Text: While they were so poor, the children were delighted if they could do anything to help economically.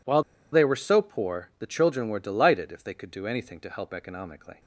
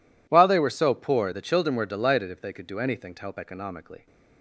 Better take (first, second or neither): second